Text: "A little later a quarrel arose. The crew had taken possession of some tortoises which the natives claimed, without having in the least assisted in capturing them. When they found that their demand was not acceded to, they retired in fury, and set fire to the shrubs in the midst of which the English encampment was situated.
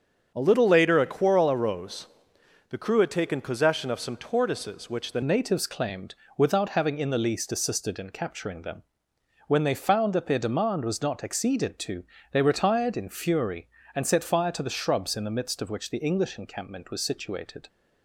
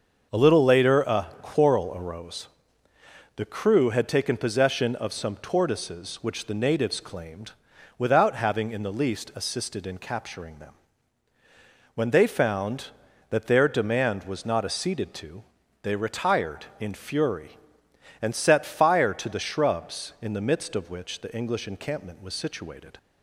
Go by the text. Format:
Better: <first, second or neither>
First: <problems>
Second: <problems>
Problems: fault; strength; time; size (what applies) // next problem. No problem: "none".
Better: second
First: starts louder than the rest; strong; until 1.3 s; 7.5 dB // changes voice at "natives"; from 5.2 s on; 12.4 s long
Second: starts louder than the rest; until 1.4 s; 6.5 dB